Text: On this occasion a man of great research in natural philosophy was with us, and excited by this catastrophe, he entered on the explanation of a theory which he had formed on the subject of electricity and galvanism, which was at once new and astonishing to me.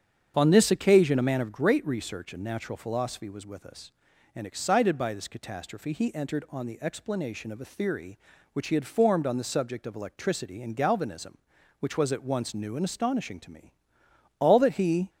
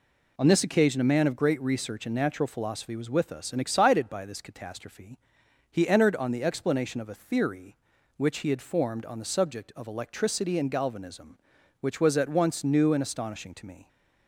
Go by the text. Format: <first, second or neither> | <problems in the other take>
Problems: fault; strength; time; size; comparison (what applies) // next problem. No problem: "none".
second | starts louder than the rest; strong; until 1.3 s; 7.5 dB // goes on to say "All that he"; noticeable; from 14.3 s on; 0.70 s long